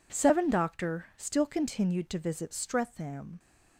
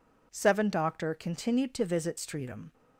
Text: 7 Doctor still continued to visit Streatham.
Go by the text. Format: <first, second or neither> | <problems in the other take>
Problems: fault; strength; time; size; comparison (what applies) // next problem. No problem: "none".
first | skips "still"; at 1.1 s